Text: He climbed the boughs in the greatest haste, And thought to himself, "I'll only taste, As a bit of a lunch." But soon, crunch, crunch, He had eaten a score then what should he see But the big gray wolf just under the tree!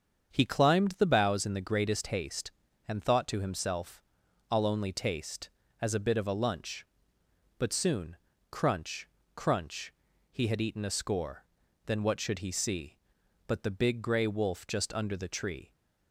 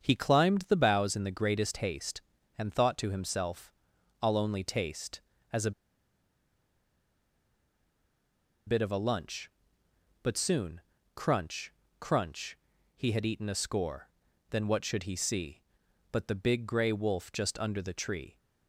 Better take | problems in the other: first | starts louder than the rest; strong; until 1.0 s; 7 dB; strong in the first // pauses between "a" and "bit"; strong; at 5.7 s; 2.9 s long // pauses between "score" and "then"; at 14.0 s; 0.42 s long; also in the first

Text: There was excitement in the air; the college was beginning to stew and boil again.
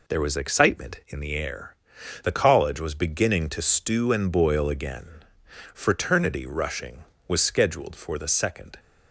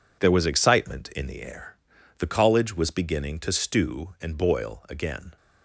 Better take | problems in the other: second | goes on to say "Fraternity rushing was scheduled for the second"; strong; from 5.7 s on; 3.0 s long

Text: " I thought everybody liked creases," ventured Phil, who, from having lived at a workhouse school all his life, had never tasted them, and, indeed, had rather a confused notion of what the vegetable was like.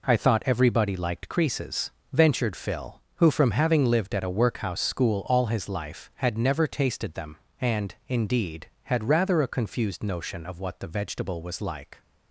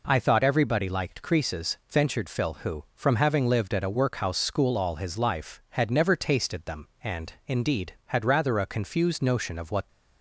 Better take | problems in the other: first | stops before "the vegetable was like"; at 9.8 s

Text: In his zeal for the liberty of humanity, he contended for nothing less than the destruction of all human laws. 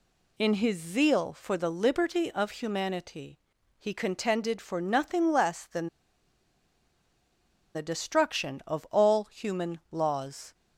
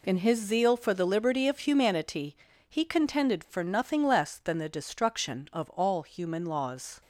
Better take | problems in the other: second | pauses between "than" and "the"; strong; at 5.8 s; 1.8 s long

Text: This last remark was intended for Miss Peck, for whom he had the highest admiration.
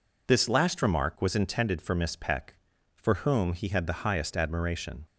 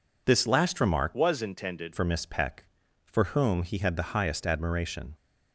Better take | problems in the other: first | changes voice from "was" to "intended"; from 1.1 to 1.9 s; 0.8 s long

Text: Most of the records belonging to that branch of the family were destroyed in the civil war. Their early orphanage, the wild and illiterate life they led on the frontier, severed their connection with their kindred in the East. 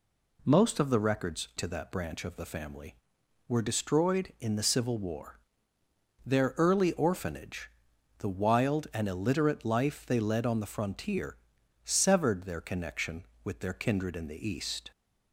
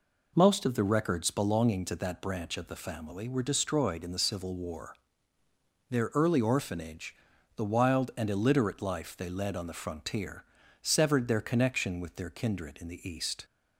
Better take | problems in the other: second | skips "belonging"; at 1.5 s

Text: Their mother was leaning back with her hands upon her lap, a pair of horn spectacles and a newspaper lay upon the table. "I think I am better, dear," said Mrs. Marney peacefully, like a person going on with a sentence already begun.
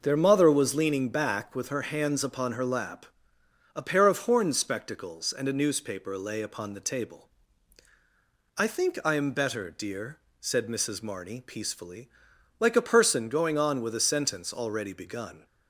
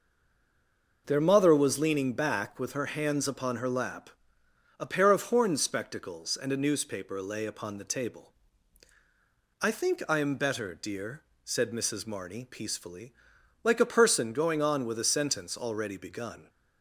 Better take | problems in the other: first | stays silent before the first word; until 1.0 s; 1.0 s long

